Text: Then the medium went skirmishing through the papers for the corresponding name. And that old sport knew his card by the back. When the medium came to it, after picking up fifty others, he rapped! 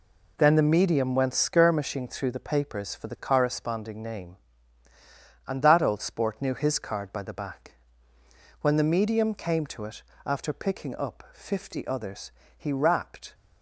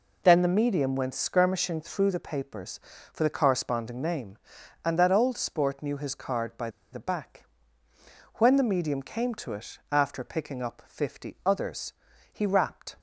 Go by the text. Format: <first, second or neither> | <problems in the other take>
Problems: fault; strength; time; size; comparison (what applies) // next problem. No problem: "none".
first | pauses between "by" and "the"; slight; at 6.6 s; 0.23 s long